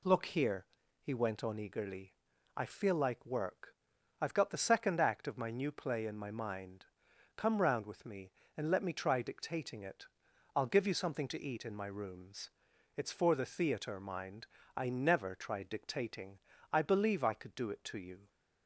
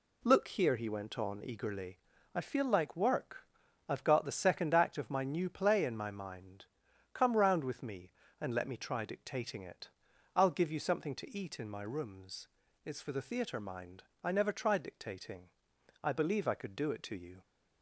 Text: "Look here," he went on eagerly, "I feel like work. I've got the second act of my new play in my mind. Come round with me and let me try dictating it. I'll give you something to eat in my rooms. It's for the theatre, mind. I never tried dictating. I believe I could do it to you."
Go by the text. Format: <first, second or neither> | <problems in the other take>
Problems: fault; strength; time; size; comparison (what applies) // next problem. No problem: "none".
neither | none